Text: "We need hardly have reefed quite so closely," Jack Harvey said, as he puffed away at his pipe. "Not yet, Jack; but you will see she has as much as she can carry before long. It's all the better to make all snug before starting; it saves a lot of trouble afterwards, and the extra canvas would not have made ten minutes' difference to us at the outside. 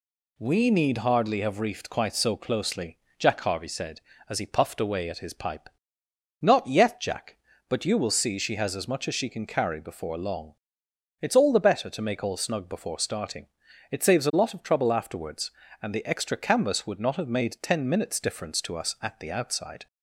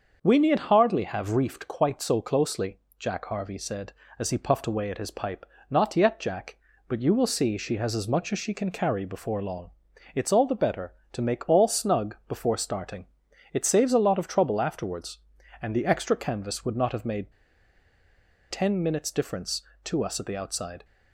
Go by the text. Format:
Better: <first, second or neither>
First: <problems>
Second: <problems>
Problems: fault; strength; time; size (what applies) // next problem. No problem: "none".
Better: first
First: none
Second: starts louder than the rest; until 1.2 s; 6.5 dB // pauses between "made" and "ten"; at 17.3 s; 1.1 s long